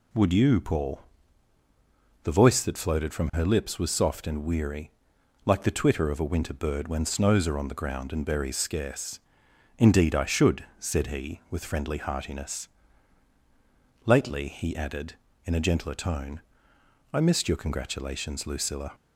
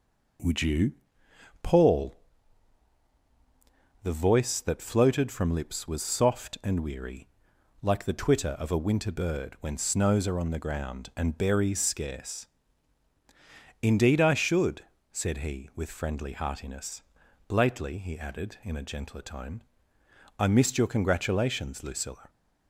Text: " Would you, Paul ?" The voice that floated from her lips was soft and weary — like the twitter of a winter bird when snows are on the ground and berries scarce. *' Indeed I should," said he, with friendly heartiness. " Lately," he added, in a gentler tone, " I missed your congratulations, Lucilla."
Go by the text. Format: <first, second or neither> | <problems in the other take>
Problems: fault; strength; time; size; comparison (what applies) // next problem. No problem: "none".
first | skips "her"; at 5.5 s